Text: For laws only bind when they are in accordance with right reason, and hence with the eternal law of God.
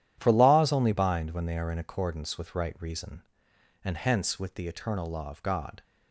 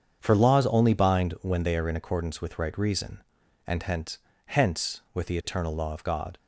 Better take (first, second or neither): first